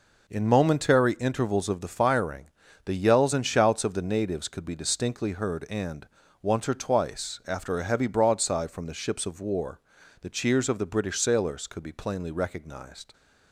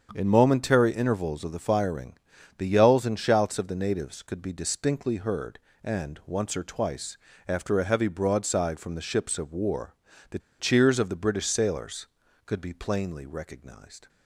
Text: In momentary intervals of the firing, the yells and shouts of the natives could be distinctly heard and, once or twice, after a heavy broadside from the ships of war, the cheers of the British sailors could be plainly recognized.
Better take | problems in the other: first | starts louder than the rest; strong; until 1.1 s; 7.5 dB // pauses between "the" and "cheers"; slight; at 10.3 s; 0.19 s long

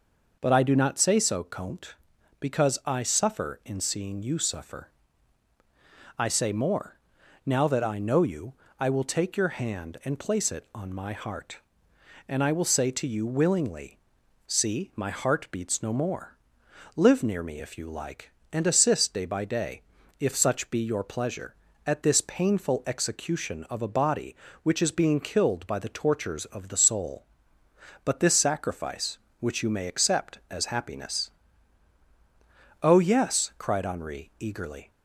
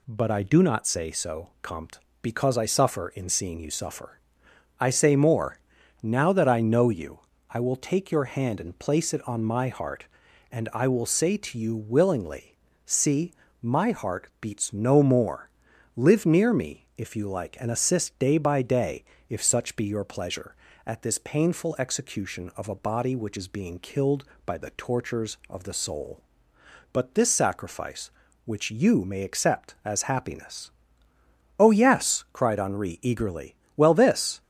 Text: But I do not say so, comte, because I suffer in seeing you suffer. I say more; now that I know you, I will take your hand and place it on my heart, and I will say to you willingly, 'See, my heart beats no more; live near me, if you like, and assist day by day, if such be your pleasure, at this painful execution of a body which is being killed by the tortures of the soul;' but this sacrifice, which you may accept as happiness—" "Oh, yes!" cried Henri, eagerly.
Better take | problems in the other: first | goes on to say "Well this"; noticeable; from 33.7 s on; 0.66 s long

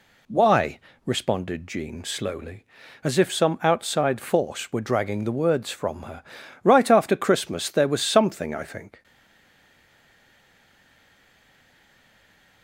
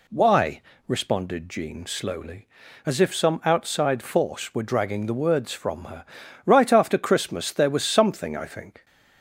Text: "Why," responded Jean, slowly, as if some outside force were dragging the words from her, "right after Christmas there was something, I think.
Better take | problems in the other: second | stays silent after the last word; strong; from 9.0 s on; 3.6 s long

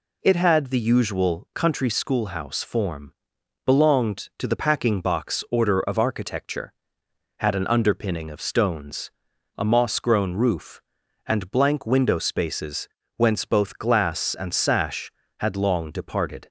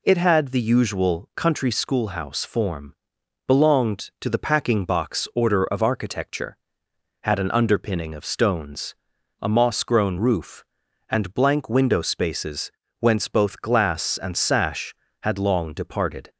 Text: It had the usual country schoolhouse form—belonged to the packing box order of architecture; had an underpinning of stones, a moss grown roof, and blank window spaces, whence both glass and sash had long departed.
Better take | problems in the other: neither | none

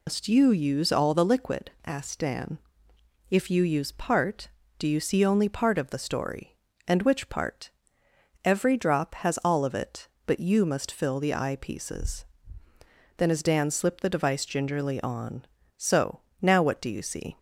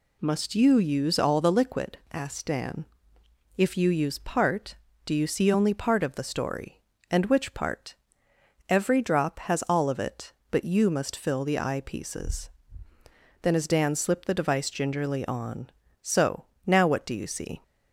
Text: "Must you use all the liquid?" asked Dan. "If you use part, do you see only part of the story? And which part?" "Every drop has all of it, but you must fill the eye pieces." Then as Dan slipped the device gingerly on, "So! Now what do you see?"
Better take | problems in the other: second | loses the start of "Must"; at 0.0 s; 135 ms

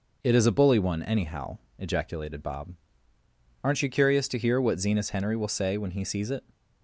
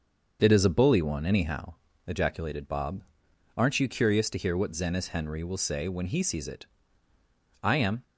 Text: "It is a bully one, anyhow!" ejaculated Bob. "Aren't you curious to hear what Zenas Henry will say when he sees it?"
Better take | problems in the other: first | starts louder than the rest; until 1.4 s; 6.5 dB // goes on to say "I am"; slight; from 7.6 s on; 0.40 s long

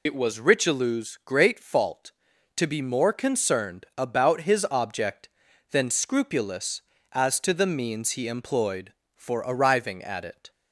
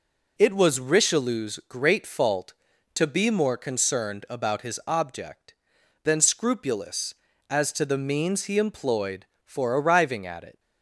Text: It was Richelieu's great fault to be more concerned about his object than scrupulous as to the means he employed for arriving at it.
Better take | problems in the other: second | loses the start of "It"; at 0.0 s; 50 ms

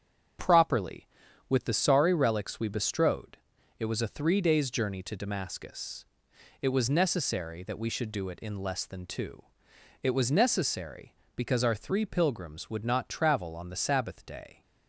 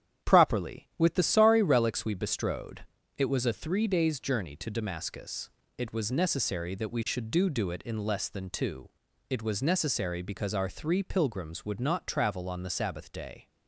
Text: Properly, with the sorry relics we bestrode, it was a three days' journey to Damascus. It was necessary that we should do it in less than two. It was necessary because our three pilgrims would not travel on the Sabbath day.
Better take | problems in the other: first | starts louder than the rest; strong; until 1.3 s; 9.5 dB; also in the first // says "do" twice; at 7.4 s

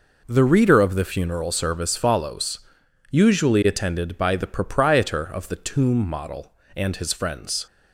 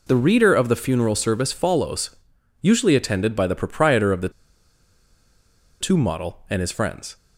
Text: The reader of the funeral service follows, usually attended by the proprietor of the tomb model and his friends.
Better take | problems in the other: first | pauses between "the" and "tomb"; strong; at 4.2 s; 1.5 s long

